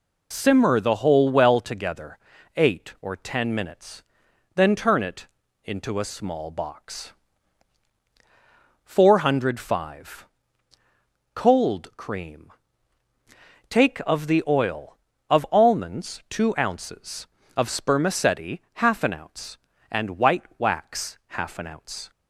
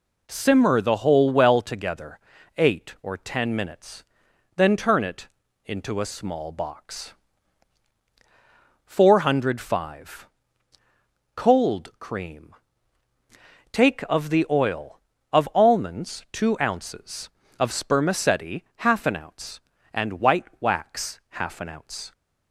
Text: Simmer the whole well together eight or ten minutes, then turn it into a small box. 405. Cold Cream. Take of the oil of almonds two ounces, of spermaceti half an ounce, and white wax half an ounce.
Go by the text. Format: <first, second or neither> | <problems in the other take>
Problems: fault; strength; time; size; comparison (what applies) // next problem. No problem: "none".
second | loses the start of "Simmer"; at 0.3 s; 25 ms // pauses between "together" and "eight"; at 2.1 s; 0.38 s long; also in the second // pauses between "it" and "into"; at 5.2 s; 0.38 s long; also in the second